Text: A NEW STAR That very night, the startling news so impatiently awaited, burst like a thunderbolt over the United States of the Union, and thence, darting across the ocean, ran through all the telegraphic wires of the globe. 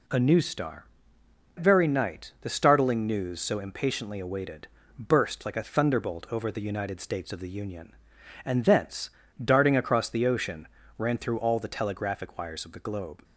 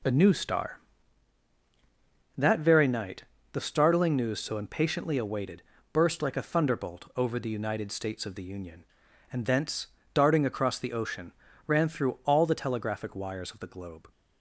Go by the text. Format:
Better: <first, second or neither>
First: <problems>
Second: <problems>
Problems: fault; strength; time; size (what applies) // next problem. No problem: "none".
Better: second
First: skips "That"; at 1.2 s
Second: none